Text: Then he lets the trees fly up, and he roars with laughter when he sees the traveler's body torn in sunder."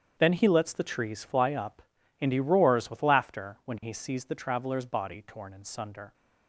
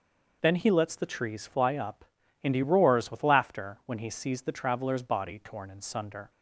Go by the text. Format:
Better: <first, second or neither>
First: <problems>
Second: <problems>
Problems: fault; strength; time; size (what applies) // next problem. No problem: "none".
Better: second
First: gets quieter; strong; throughout; 13 dB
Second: none